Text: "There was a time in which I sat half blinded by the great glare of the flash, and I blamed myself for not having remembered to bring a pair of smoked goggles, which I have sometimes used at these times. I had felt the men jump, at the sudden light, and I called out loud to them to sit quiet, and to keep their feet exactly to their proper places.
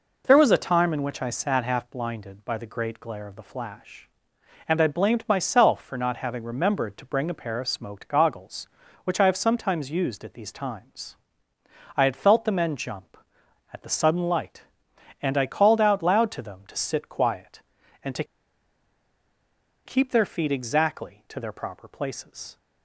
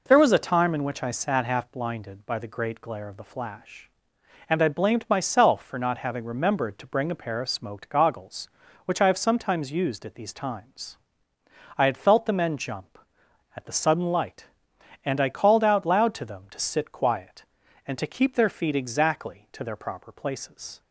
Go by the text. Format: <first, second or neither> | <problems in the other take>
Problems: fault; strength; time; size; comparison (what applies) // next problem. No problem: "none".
second | pauses between "to" and "keep"; strong; at 18.2 s; 1.6 s long